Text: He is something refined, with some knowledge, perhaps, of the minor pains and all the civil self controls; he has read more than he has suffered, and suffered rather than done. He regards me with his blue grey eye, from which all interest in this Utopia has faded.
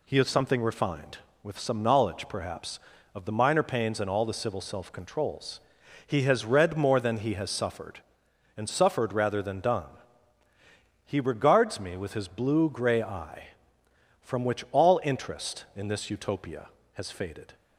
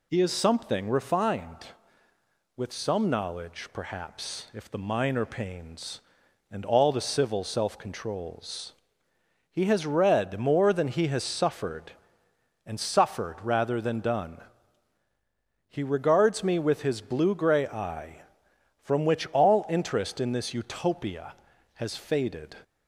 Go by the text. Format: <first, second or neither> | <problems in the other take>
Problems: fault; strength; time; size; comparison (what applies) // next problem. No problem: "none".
first | says "if" for "of"; at 4.5 s